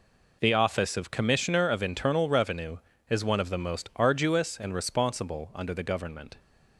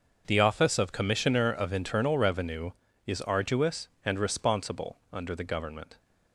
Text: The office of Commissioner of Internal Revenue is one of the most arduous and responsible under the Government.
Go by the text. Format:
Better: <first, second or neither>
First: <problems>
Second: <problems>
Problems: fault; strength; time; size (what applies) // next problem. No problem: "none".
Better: first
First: none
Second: starts louder than the rest; until 1.2 s; 6 dB // skips "one of the most"; at 3.2 s // pauses between "responsible" and "under"; slight; at 4.9 s; 0.16 s long